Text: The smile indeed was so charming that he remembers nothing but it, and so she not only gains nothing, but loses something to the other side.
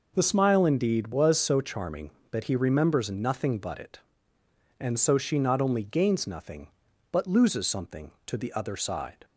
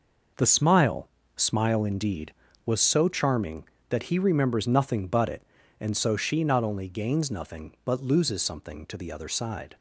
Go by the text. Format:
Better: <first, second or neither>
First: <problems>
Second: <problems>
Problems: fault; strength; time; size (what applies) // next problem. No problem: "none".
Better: first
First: none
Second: says "smile" twice; at 1.3 s